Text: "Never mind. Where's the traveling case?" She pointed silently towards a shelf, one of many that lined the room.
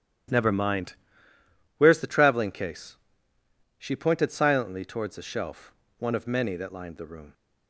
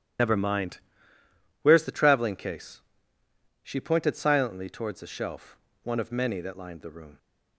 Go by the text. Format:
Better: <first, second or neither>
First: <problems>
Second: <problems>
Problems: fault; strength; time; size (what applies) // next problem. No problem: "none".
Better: first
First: starts louder than the rest; strong; until 2.1 s; 10.5 dB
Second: loses the start of "Never"; at 0.1 s; 70 ms // starts louder than the rest; strong; until 2.0 s; 11 dB